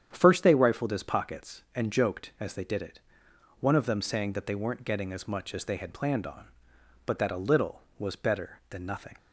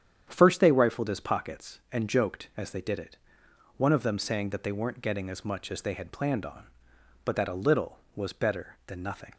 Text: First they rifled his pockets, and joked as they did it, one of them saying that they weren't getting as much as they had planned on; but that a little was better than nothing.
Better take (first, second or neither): neither